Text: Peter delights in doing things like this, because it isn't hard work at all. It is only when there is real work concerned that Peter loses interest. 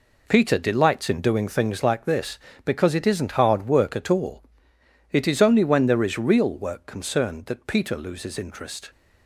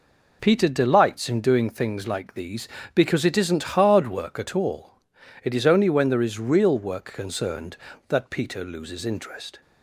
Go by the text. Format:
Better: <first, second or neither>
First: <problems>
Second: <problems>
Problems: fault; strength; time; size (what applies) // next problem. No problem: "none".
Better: first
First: none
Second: says "these" for "this"; at 2.3 s